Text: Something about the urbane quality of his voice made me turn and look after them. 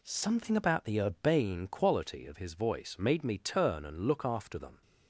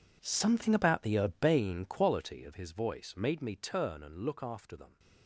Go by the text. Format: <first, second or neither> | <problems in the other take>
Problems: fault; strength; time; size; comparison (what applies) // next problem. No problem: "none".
first | gets quieter; strong; throughout; 16 dB